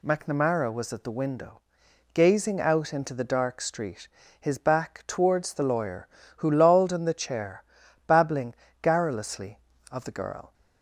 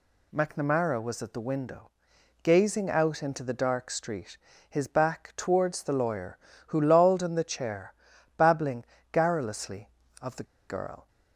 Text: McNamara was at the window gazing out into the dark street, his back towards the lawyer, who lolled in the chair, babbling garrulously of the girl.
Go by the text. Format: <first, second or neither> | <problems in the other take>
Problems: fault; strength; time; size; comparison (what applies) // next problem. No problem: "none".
first | pauses between "window" and "gazing"; noticeable; at 1.9 s; 0.50 s long; noticeable in the first // pauses between "babbling" and "garrulously"; slight; at 8.8 s; 0.26 s long; slight in the first // pauses between "the" and "girl"; slight; at 10.4 s; 0.25 s long